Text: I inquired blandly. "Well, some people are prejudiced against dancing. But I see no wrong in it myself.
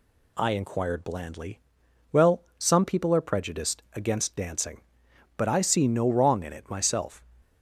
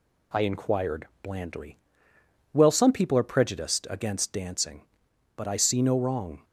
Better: first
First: none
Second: stops before "in it myself"; at 6.4 s

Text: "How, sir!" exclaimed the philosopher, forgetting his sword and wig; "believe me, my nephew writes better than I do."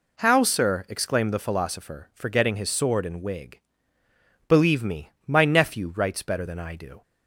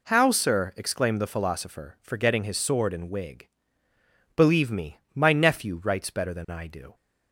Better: neither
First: none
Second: none

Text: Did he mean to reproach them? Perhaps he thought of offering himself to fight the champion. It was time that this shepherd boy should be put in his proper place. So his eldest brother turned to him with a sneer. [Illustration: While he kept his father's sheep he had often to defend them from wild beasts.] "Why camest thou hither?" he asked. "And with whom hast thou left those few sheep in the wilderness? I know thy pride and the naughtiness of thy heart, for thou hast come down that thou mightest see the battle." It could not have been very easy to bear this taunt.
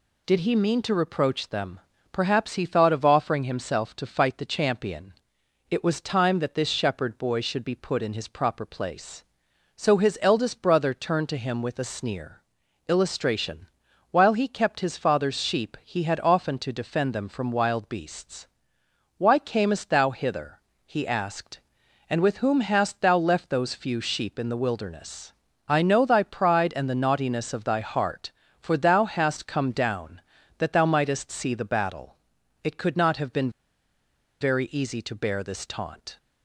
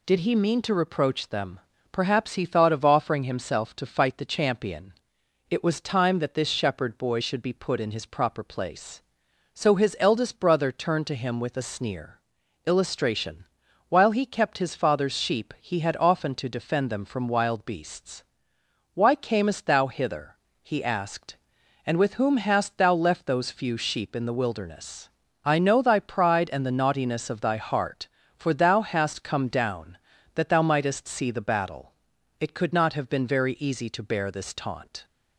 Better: second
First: pauses between "been" and "very"; noticeable; at 33.5 s; 0.90 s long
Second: none

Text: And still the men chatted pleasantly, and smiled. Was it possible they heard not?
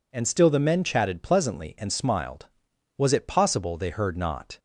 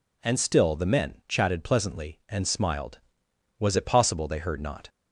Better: neither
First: none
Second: none

